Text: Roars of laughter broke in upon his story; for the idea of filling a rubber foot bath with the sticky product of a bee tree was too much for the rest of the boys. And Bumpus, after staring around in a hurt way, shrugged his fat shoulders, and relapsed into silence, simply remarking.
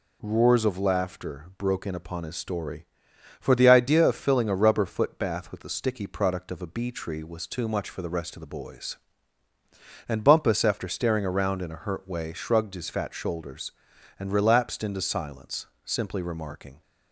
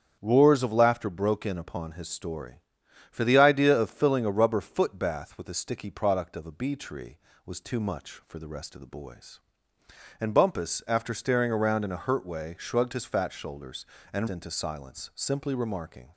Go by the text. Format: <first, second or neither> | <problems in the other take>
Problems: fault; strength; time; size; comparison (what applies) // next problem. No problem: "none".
first | starts louder than the rest; strong; until 1.2 s; 8 dB // skips "relapsed"; at 14.2 s